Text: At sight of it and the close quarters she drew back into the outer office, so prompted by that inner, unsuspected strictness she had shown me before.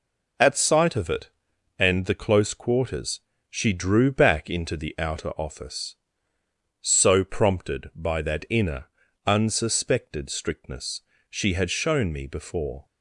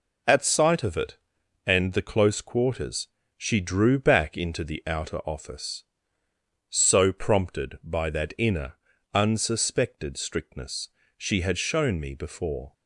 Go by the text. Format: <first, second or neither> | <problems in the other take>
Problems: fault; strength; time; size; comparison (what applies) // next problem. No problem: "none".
neither | pauses between "quarters" and "she"; slight; the same in both // pauses between "strictness" and "she"; slight; the same in both